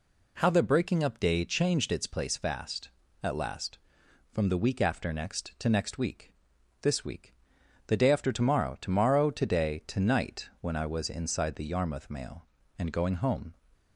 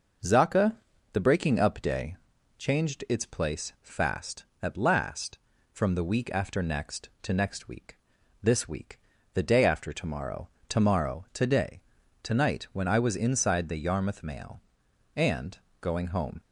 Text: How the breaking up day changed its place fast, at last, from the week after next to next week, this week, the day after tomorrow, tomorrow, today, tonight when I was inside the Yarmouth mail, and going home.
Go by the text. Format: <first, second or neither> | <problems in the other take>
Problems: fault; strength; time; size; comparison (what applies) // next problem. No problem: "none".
first | says "Zaka" for "How"; at 0.2 s // pauses between "day" and "changed"; at 2.1 s; 0.42 s long // pauses between "and" and "going"; slight; at 15.5 s; 0.22 s long